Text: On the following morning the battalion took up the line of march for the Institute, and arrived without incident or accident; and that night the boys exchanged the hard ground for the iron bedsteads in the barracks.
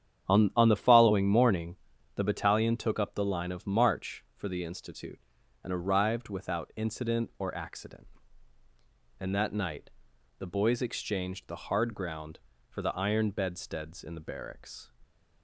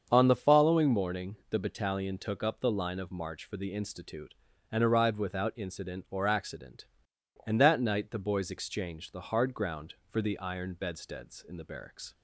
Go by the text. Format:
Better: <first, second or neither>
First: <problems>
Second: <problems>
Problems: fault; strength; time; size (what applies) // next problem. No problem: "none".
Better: second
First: starts louder than the rest; strong; until 1.3 s; 9 dB // says "On" twice; at 0.5 s // pauses between "morning" and "the"; at 1.7 s; 0.40 s long // pauses between "night" and "the"; noticeable; at 9.9 s; 0.48 s long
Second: starts louder than the rest; until 1.1 s; 7 dB